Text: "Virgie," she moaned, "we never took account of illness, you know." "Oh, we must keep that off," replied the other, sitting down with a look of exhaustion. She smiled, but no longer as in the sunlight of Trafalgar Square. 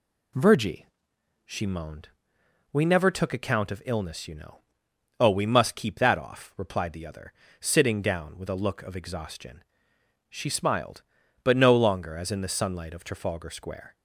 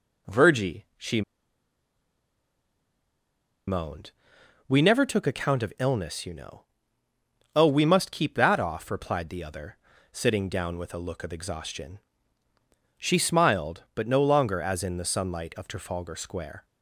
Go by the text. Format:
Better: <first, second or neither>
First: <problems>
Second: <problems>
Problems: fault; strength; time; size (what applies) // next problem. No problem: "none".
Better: first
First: none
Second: pauses between "she" and "moaned"; strong; at 1.2 s; 2.4 s long